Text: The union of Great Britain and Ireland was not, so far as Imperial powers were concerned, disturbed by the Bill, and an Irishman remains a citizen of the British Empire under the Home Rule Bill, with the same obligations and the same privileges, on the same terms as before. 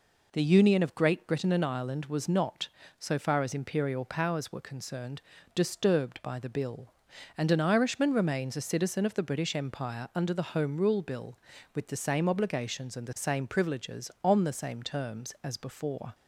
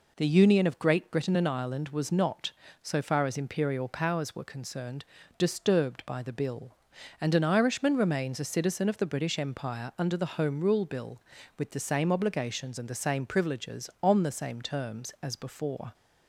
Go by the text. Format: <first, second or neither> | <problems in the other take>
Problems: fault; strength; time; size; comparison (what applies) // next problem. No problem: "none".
neither | none